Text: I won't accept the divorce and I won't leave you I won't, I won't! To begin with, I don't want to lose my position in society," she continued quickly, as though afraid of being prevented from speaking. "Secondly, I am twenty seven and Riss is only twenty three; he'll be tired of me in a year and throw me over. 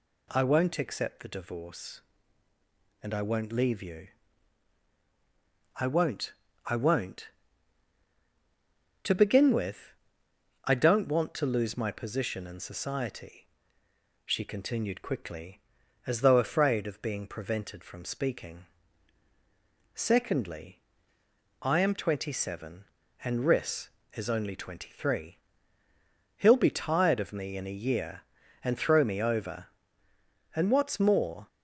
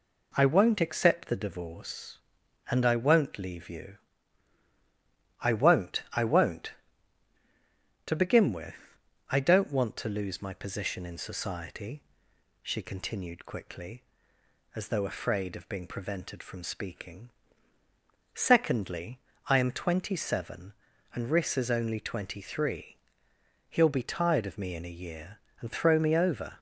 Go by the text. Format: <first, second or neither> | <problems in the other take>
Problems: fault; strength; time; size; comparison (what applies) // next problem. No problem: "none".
second | pauses between "you" and "I"; strong; at 4.0 s; 1.7 s long; strong in the second // goes on to say "And what's more"; noticeable; from 30.5 s on; 0.94 s long